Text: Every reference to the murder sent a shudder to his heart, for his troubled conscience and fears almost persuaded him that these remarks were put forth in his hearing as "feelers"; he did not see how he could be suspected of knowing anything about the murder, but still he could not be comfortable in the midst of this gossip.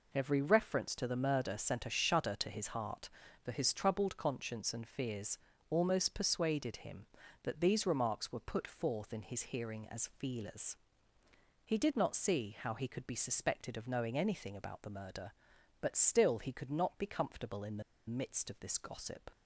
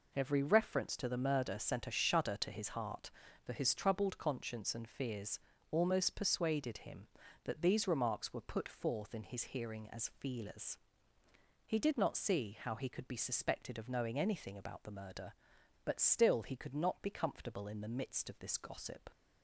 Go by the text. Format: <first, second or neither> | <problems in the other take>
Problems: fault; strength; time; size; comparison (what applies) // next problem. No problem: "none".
second | pauses between "fears" and "almost"; slight; at 5.3 s; 0.32 s long; slight in the second // pauses between "the" and "midst"; slight; at 17.8 s; 0.26 s long